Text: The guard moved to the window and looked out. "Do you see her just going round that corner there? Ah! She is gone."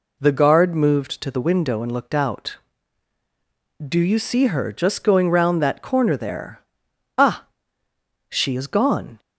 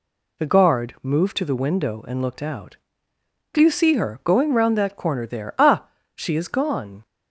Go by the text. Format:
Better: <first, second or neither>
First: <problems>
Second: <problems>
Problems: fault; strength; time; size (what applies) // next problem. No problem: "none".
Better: first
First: none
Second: skips "just"; at 4.2 s